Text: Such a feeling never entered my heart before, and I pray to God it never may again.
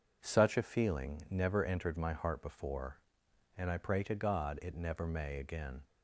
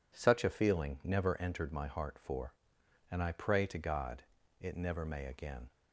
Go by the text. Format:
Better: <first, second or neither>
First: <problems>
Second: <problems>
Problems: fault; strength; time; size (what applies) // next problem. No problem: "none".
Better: first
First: none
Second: says "for" for "before"; at 2.1 s // pauses between "God" and "it"; at 4.2 s; 0.40 s long